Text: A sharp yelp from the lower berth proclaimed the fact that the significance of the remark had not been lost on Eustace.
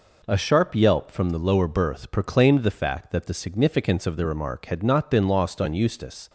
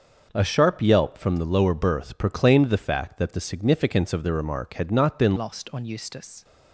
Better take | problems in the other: first | starts louder than the rest; until 1.3 s; 6 dB // changes voice at "lost"; from 5.3 s on; 1.1 s long

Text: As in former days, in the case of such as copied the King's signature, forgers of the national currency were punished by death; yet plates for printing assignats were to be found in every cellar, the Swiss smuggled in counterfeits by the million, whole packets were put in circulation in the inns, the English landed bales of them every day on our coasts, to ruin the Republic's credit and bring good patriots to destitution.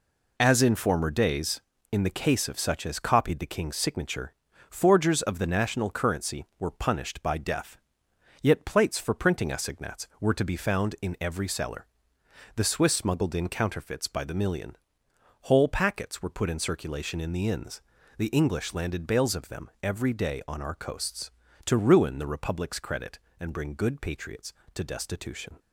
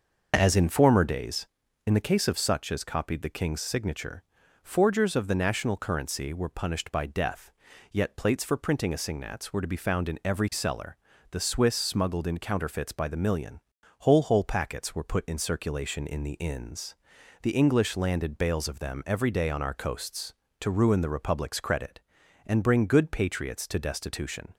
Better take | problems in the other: first | says "whole" twice; at 14.2 s

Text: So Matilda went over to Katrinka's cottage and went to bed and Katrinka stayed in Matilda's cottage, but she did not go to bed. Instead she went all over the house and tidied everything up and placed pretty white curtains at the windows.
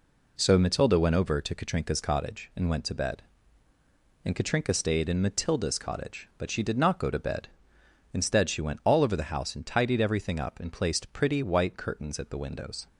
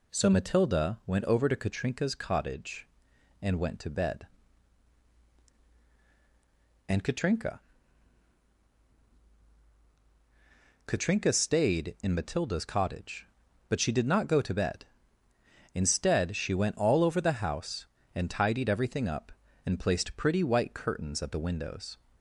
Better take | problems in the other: first | says "Katrinka" twice; at 10.8 s

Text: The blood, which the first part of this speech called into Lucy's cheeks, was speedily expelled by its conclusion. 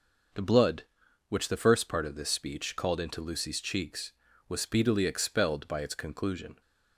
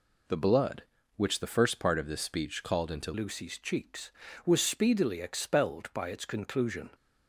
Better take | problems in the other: first | changes voice at "Lucy's"; from 3.1 s on; 3.7 s long

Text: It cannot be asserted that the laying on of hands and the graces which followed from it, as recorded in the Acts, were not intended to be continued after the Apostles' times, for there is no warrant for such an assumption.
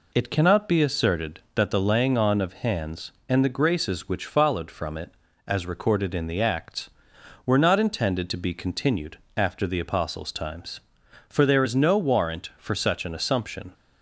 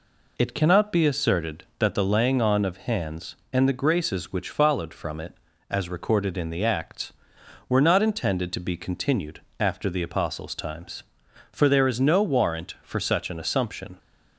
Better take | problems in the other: neither | pauses between "continued" and "after"; slight; the same in both

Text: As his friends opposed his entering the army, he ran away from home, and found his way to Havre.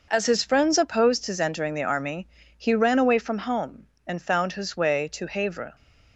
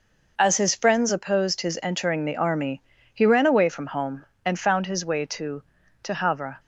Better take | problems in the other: first | says "to" twice; at 6.0 s

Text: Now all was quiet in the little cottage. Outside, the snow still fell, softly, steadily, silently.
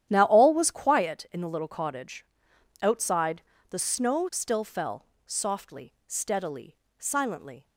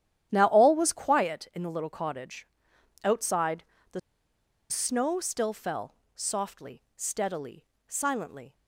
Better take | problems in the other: first | starts louder than the rest; strong; until 1.3 s; 10.5 dB; strong in the first // pauses between "the" and "snow"; noticeable; at 3.9 s; 0.70 s long

